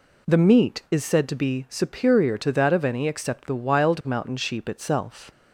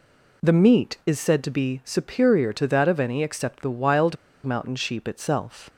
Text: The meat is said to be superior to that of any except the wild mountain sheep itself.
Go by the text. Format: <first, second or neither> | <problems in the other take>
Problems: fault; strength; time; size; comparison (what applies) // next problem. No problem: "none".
first | pauses between "wild" and "mountain"; slight; at 4.1 s; 0.29 s long